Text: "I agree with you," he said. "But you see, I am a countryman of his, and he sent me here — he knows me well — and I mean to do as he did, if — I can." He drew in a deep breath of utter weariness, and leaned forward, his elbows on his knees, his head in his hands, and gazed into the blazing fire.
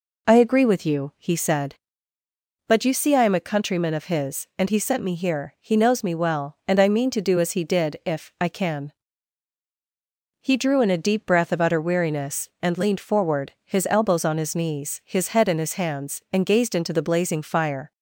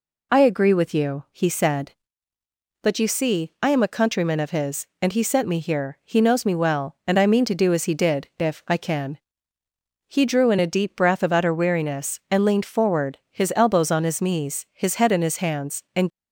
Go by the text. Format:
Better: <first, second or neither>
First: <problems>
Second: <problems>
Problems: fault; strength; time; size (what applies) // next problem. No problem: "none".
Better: first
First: none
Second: stops before "gazed into the blazing fire"; at 16.1 s